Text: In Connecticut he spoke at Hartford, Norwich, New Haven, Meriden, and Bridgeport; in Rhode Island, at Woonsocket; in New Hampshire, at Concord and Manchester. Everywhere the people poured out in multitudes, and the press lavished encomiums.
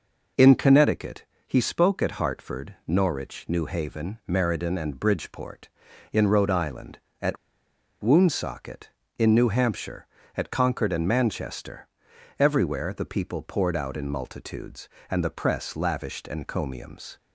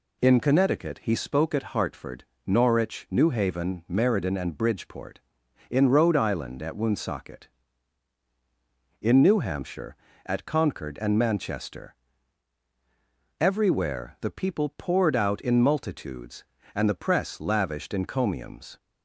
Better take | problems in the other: second | pauses between "Connecticut" and "he"; slight; at 1.2 s; 0.24 s long // pauses between "at" and "Woonsocket"; noticeable; at 7.3 s; 0.65 s long

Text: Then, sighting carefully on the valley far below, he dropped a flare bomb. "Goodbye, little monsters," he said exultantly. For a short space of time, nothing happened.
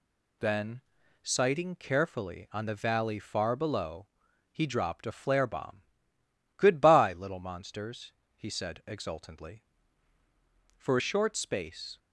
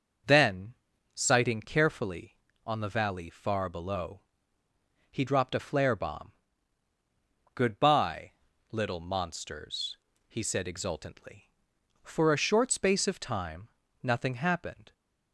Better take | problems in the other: second | stops before "of time nothing happened"; at 11.9 s

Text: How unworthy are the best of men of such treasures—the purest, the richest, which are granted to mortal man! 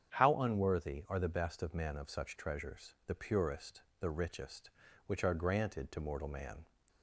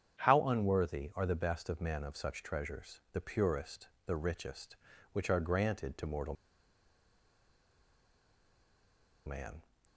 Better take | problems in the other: first | starts louder than the rest; strong; until 1.3 s; 8.5 dB; strong in the first // pauses between "mortal" and "man"; strong; at 6.3 s; 2.9 s long

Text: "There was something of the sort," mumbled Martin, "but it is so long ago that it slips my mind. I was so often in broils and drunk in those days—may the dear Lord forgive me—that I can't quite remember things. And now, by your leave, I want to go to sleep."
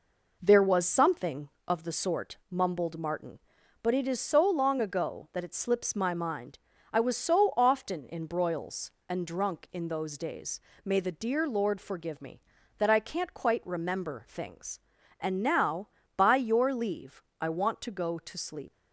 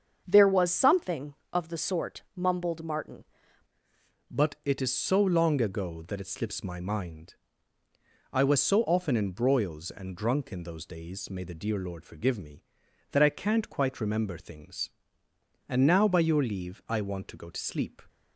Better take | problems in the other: first | starts louder than the rest; until 1.2 s; 7 dB // changes voice at "but"; from 4.2 s on; 13.8 s long

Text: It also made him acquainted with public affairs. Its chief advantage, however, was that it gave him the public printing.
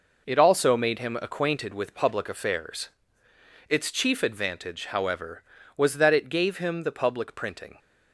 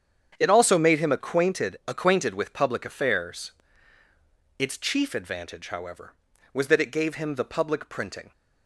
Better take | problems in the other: first | starts louder than the rest; strong; until 1.4 s; 8 dB // says "acquainted" twice; at 1.8 s

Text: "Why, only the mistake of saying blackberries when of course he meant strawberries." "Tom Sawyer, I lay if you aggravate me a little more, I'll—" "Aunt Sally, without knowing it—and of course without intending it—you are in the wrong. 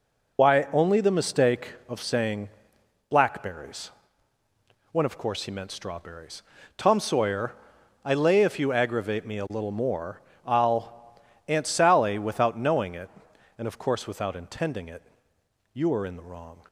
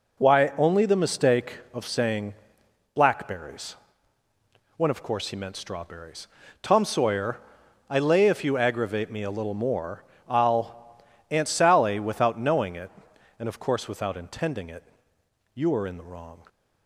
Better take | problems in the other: second | loses the start of "Why"; at 0.3 s; 60 ms // pauses between "saying" and "blackberries"; noticeable; at 2.4 s; 0.60 s long; noticeable in the second // pauses between "blackberries" and "when"; at 3.9 s; 1.0 s long; also in the second

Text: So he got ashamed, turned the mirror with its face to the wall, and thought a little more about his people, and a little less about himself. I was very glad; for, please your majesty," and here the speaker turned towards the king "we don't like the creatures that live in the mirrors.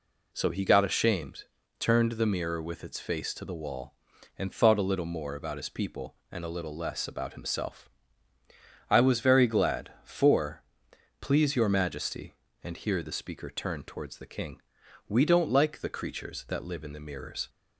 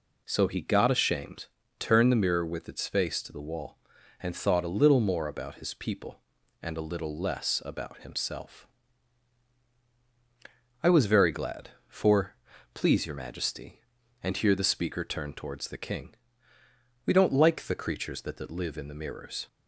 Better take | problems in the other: first | pauses between "king" and "we"; noticeable; at 16.1 s; 0.90 s long; also in the first // says "that" twice; at 18.3 s

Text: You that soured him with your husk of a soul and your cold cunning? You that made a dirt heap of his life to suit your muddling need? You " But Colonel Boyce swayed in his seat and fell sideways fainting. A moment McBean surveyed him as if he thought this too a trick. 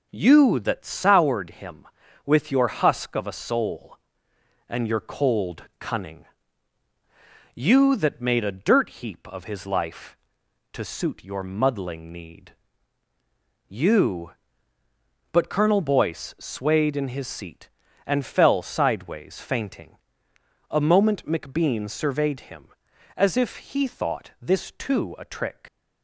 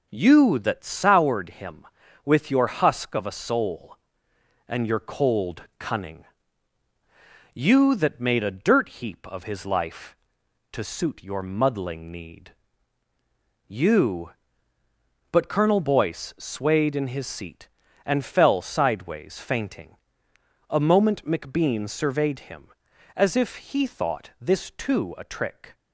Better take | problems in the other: second | leaves "trick" unfinished; at 25.6 s; 65 ms

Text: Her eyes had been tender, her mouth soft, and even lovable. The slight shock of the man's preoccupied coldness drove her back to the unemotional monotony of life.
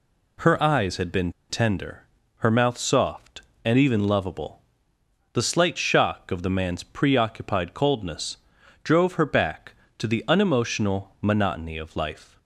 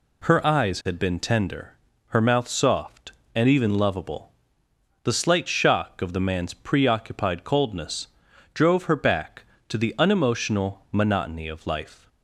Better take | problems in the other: second | pauses between "been" and "tender"; slight; at 1.3 s; 0.17 s long // pauses between "coldness" and "drove"; at 8.3 s; 0.44 s long; also in the second

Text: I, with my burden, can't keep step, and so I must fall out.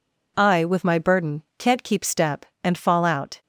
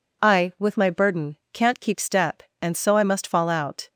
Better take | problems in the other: second | skips "so I must"; at 2.7 s

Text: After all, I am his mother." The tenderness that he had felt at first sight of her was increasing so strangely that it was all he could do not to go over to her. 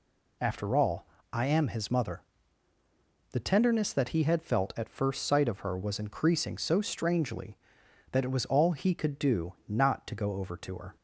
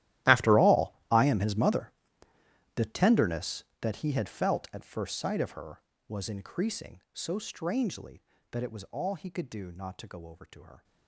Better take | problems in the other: first | gets quieter; strong; throughout; 19 dB

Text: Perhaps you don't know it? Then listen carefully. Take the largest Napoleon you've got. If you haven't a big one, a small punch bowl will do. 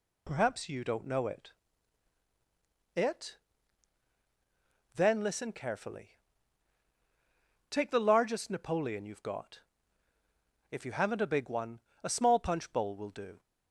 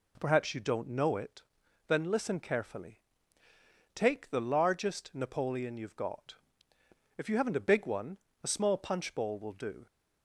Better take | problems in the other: second | says "it" twice; at 2.9 s

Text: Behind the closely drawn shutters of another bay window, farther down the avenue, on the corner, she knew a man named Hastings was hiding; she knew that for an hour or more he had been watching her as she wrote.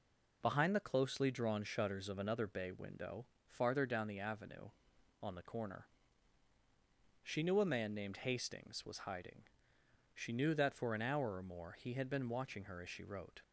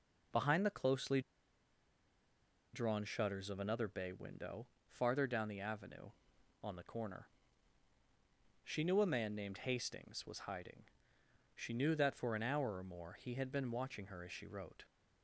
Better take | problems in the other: first | pauses between "closely" and "drawn"; strong; at 1.2 s; 1.5 s long

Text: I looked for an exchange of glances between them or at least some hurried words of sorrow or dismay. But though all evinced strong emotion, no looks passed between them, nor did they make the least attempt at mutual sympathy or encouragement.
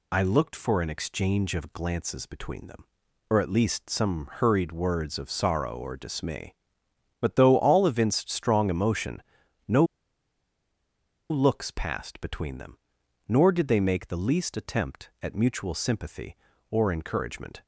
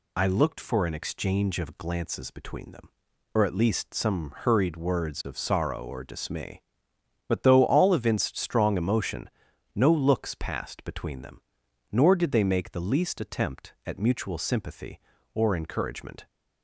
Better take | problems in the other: second | pauses between "no" and "looks"; strong; at 9.8 s; 1.4 s long

